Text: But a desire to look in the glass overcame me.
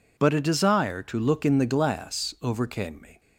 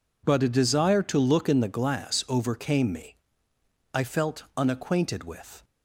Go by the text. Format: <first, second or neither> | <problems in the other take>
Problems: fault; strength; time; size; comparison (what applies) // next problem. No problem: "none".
first | goes on to say "I felt unacquainted with"; strong; from 3.9 s on; 1.7 s long